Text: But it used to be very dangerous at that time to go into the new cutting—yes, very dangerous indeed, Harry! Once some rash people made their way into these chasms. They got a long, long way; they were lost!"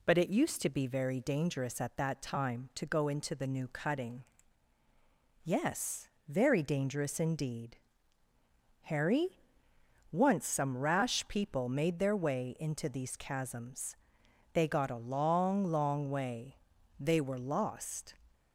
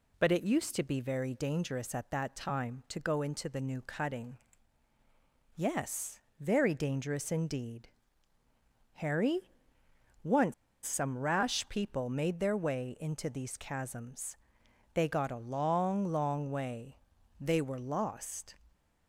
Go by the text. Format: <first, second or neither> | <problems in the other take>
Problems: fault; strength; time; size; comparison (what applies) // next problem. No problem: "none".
first | pauses between "Once" and "some"; slight; at 10.5 s; 0.31 s long